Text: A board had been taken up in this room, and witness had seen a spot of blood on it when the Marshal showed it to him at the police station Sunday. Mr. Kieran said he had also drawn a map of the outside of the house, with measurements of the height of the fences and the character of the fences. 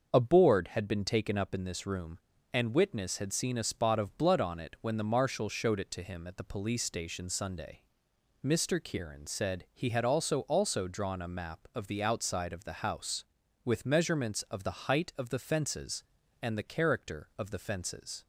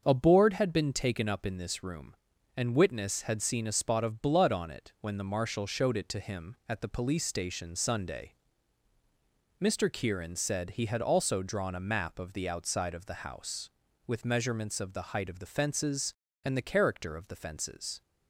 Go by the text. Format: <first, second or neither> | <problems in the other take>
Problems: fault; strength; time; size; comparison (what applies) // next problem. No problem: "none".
second | starts louder than the rest; until 1.1 s; 6.5 dB; also in the second // says "also" twice; at 10.4 s